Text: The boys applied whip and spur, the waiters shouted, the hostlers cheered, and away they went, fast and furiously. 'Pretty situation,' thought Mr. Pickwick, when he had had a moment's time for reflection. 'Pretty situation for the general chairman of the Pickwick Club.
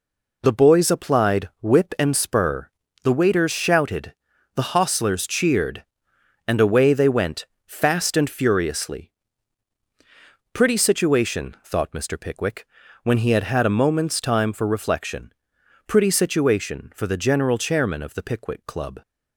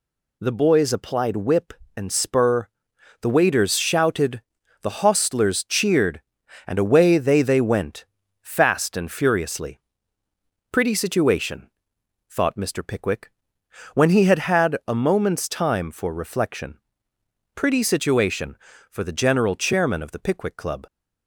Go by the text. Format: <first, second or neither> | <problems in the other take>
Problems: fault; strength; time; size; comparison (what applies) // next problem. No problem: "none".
first | says "they" twice; at 7.4 s